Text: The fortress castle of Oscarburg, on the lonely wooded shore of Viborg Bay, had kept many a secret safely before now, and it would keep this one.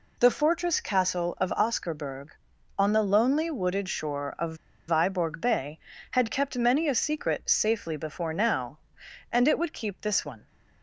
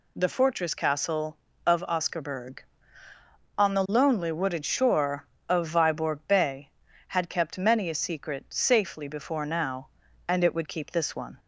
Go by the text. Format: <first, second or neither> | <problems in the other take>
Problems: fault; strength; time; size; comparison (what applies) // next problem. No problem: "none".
second | pauses between "of" and "Viborg"; slight; at 4.5 s; 0.32 s long